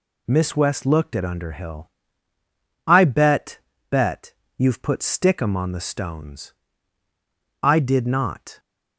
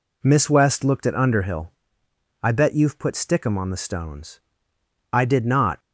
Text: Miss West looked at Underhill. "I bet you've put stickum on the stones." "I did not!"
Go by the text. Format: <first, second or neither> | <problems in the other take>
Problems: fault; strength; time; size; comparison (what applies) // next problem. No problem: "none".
second | says "bet" twice; at 3.9 s